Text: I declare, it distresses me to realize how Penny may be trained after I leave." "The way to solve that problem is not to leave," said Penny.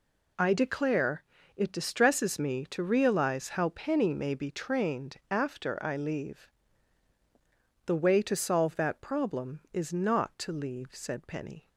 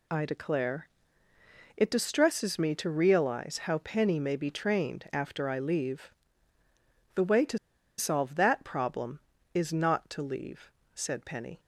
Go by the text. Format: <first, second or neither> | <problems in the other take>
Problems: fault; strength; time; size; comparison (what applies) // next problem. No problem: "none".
first | pauses between "to" and "solve"; at 7.5 s; 0.40 s long